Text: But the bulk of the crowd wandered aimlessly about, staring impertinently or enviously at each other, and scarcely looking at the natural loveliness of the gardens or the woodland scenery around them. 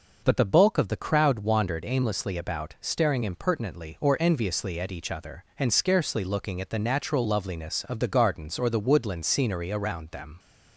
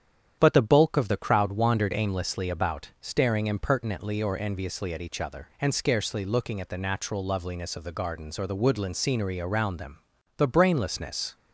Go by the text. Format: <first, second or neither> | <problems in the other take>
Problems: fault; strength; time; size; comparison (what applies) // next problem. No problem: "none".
first | starts louder than the rest; strong; until 1.4 s; 9.5 dB // goes on to say "The brainlessness"; noticeable; from 10.3 s on; 0.98 s long